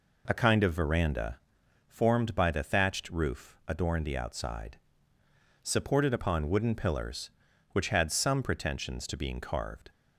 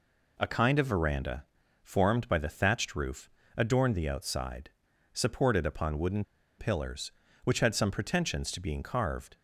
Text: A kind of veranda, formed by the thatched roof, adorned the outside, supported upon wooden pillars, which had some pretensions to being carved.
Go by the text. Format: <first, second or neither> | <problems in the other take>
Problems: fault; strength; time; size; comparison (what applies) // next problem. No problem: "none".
first | pauses between "wooden" and "pillars"; slight; at 6.2 s; 0.35 s long